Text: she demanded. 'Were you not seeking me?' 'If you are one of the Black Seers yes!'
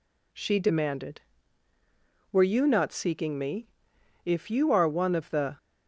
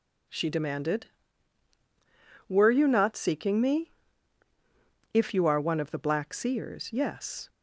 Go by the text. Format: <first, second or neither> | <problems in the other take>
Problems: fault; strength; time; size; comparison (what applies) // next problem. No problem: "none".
second | stops before "Black Seers yes"; at 5.5 s